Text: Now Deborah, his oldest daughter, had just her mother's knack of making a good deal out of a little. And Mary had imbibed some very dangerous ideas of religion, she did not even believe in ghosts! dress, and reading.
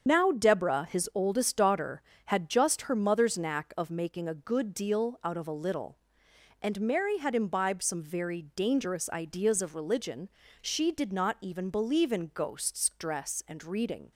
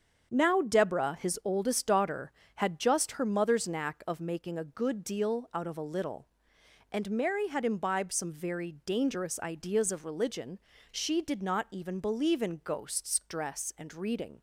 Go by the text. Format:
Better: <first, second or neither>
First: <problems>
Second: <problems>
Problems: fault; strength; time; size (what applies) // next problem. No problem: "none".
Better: second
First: loses the start of "Now"; at 0.0 s; 50 ms // starts louder than the rest; strong; until 1.0 s; 7 dB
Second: starts louder than the rest; strong; until 1.3 s; 7 dB